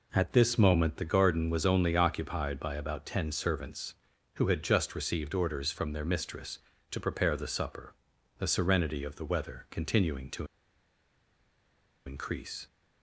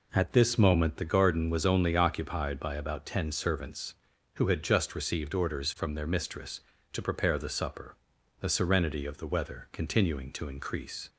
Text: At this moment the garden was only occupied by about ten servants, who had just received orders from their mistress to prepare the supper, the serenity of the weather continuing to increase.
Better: second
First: pauses between "to" and "increase"; strong; at 10.4 s; 1.5 s long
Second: none

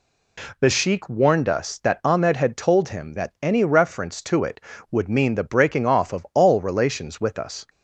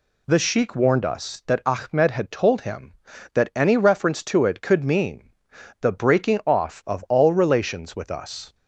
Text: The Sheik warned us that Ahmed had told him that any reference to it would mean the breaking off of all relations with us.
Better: first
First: none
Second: says "could" for "would"; at 4.6 s // pauses between "mean" and "the"; noticeable; at 5.2 s; 0.52 s long

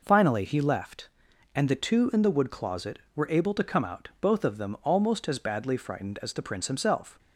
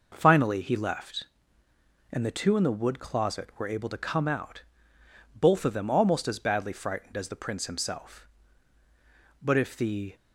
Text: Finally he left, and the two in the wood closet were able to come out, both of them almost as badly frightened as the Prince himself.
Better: first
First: none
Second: goes on to say "But if the"; noticeable; from 9.4 s on; 0.74 s long

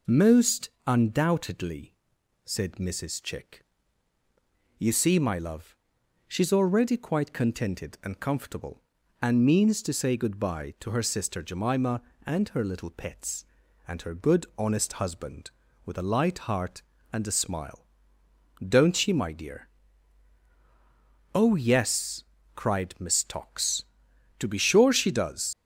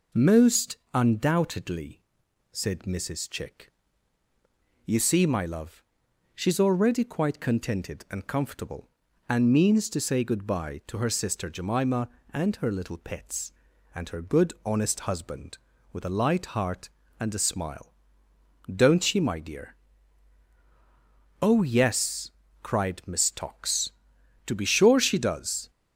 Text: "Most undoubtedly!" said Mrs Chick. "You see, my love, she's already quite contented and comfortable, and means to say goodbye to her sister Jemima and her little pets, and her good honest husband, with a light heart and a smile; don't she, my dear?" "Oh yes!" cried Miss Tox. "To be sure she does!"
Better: second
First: pauses between "Most" and "undoubtedly"; slight; at 0.6 s; 0.16 s long // leaves "does" unfinished; at 25.5 s; 95 ms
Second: pauses between "Most" and "undoubtedly"; slight; at 0.7 s; 0.16 s long

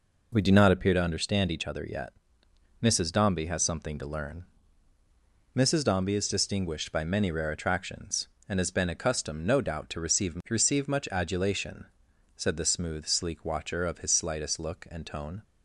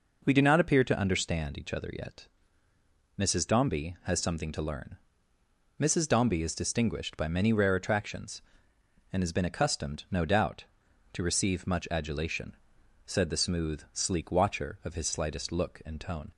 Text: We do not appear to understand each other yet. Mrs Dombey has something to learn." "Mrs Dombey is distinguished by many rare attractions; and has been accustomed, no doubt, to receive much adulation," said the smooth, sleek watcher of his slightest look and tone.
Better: second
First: says "receive" twice; at 10.4 s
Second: none

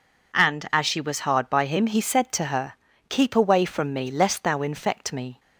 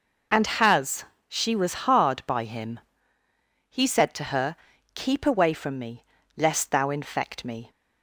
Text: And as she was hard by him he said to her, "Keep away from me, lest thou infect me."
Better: first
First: none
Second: says "has" for "as"; at 0.4 s // pauses between "him" and "he"; noticeable; at 2.8 s; 0.88 s long

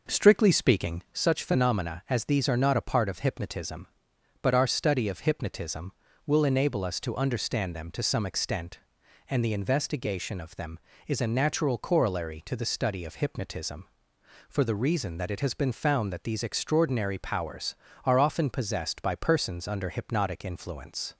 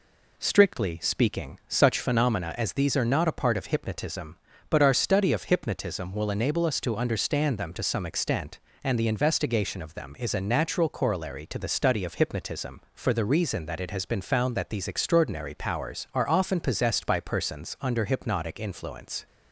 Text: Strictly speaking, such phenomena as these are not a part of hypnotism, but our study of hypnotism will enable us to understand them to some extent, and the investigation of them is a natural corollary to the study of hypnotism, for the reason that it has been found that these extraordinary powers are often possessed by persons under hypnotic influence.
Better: second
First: starts louder than the rest; noticeable; until 1.3 s; 5.5 dB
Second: none

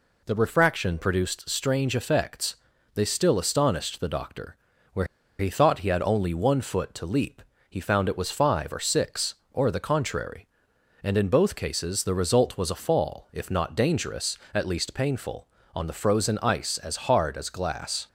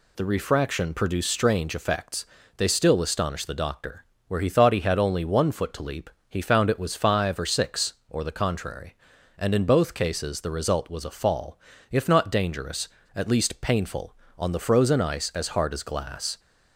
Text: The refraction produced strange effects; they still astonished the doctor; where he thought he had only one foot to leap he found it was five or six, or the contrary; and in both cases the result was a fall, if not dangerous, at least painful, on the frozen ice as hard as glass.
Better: second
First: pauses between "where" and "he"; slight; at 5.0 s; 0.34 s long // pauses between "leap" and "he"; slight; at 7.4 s; 0.26 s long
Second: pauses between "leap" and "he"; slight; at 6.0 s; 0.22 s long

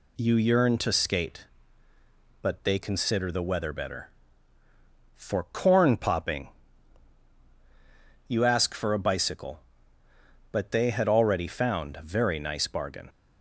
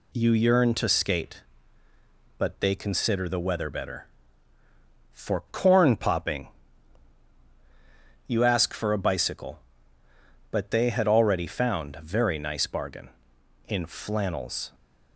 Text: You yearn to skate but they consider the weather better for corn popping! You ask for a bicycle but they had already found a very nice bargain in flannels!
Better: second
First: stops before "in flannels"; at 13.0 s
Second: none

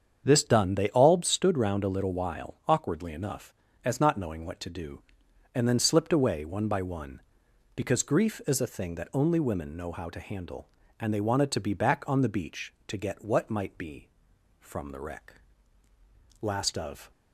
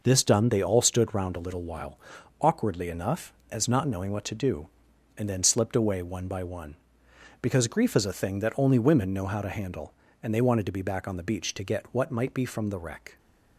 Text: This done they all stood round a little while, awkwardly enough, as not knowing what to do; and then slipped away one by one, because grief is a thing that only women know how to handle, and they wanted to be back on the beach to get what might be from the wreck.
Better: second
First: starts louder than the rest; strong; until 1.2 s; 7.5 dB // goes on to say "Last of"; noticeable; from 16.4 s on; 0.70 s long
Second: none

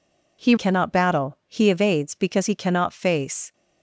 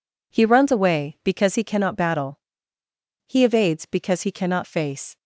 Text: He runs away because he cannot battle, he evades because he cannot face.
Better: second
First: skips "runs away because he"; at 0.5 s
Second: none

